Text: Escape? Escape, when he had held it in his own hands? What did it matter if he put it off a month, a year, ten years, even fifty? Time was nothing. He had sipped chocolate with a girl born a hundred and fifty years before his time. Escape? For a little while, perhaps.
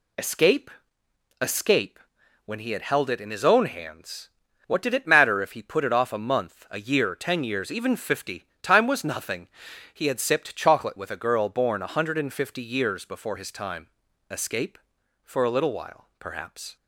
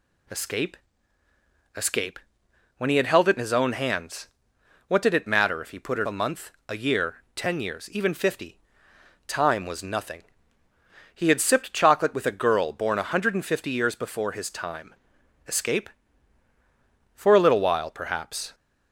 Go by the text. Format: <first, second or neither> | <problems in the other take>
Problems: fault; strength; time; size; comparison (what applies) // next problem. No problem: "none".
first | skips "off"; at 6.0 s